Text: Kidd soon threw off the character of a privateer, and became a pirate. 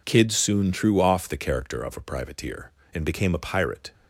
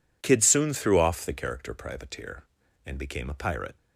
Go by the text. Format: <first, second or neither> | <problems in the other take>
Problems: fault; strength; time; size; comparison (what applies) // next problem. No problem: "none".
first | skips "of a"; at 1.7 s